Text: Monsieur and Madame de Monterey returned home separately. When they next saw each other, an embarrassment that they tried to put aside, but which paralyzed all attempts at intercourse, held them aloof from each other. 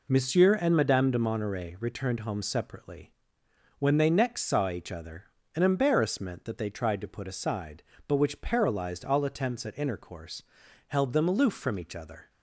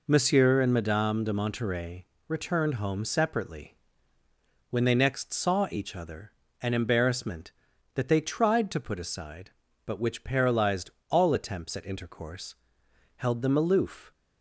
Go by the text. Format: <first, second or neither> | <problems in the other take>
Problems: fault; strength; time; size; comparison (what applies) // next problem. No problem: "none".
first | pauses between "Monterey" and "returned"; slight; at 2.0 s; 0.20 s long // pauses between "paralyzed" and "all"; slight; at 10.9 s; 0.18 s long // stops before "from each other"; at 14.1 s